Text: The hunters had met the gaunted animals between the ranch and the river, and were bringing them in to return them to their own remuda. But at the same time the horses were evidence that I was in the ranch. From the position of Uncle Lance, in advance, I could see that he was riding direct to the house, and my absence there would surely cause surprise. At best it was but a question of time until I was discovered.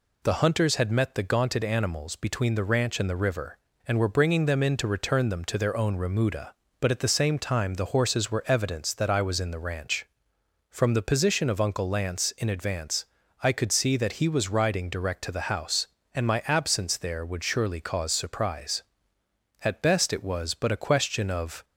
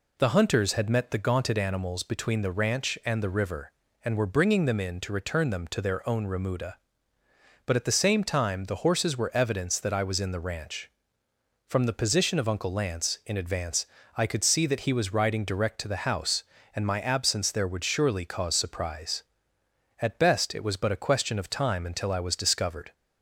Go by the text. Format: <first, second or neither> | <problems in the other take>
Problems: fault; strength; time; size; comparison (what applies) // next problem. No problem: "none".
second | stops before "time until I was discovered"; at 21.6 s